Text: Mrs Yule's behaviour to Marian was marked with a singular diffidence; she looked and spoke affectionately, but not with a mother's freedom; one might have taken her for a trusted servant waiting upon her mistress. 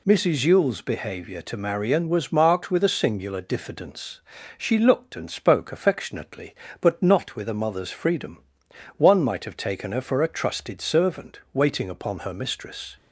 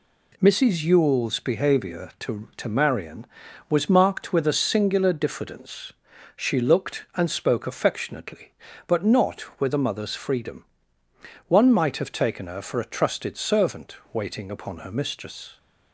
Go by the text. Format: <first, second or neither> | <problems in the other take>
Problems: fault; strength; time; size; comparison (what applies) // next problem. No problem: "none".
first | says "to" twice; at 2.5 s